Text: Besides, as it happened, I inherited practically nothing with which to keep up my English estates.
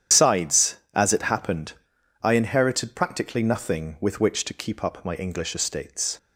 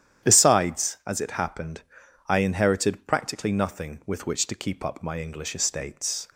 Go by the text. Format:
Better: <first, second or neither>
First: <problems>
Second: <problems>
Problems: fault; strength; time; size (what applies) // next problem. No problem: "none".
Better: second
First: loses the start of "Besides"; at 0.1 s; 105 ms // starts louder than the rest; strong; until 1.3 s; 10 dB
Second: starts louder than the rest; strong; until 1.3 s; 10.5 dB